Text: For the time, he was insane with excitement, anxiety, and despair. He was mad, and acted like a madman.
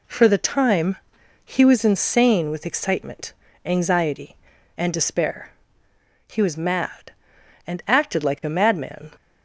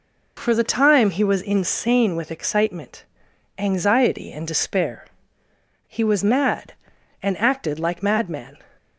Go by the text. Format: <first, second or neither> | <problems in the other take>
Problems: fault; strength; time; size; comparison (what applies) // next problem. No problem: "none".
first | skips "a"; at 8.0 s